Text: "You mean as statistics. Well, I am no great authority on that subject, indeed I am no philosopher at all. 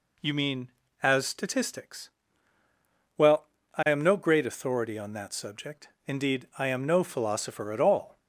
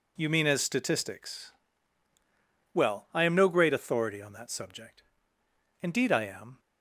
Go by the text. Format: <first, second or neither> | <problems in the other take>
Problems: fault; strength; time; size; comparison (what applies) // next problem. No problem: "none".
first | stops before "no philosopher at all"; at 6.5 s